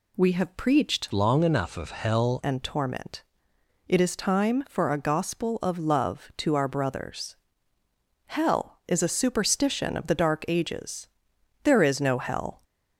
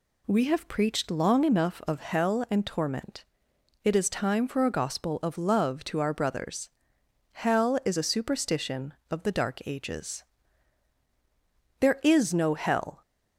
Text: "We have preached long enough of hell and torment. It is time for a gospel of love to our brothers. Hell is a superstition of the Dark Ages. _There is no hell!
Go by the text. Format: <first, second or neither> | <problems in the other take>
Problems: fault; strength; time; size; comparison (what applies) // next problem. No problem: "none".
second | changes voice from "long" to "hell"; from 1.1 to 2.4 s; 1.3 s long